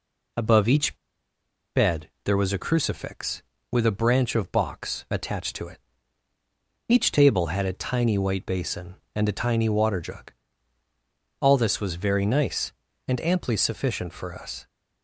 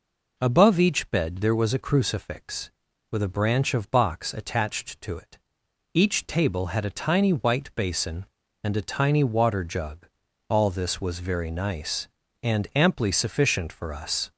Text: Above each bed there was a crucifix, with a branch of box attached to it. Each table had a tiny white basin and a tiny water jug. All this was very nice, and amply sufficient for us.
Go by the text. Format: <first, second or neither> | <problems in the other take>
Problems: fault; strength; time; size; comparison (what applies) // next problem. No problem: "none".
second | pauses between "each" and "bed"; noticeable; at 0.9 s; 0.78 s long // pauses between "bed" and "there"; slight; at 2.0 s; 0.16 s long